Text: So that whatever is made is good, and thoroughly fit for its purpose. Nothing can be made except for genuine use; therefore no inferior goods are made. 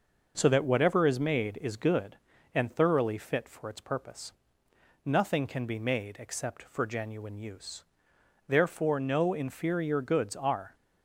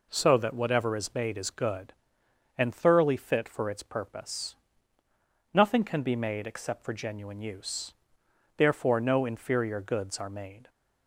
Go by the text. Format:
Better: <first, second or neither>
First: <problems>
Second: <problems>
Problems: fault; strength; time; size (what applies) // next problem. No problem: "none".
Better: second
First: stops before "made"; at 10.7 s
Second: none